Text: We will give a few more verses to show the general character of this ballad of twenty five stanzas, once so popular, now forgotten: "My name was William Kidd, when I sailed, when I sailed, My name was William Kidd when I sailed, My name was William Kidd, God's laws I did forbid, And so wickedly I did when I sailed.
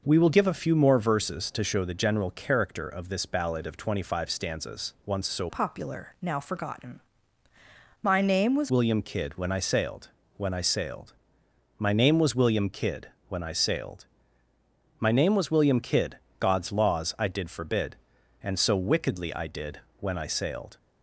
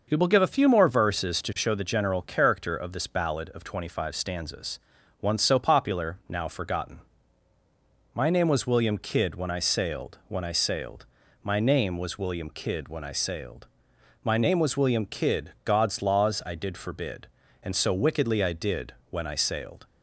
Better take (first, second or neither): second